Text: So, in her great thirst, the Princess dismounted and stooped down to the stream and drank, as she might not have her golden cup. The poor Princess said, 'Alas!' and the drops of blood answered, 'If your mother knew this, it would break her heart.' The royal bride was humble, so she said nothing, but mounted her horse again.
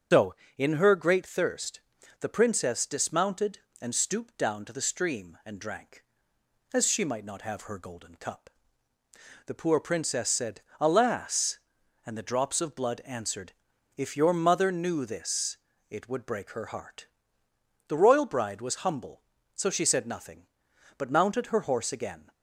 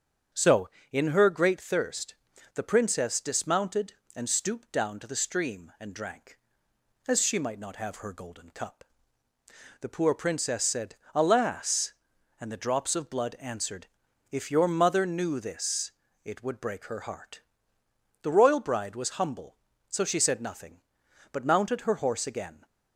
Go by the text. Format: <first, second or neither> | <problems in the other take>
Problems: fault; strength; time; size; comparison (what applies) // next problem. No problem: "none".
second | loses the start of "So"; at 0.1 s; 120 ms // starts louder than the rest; until 1.3 s; 7 dB; strong in the second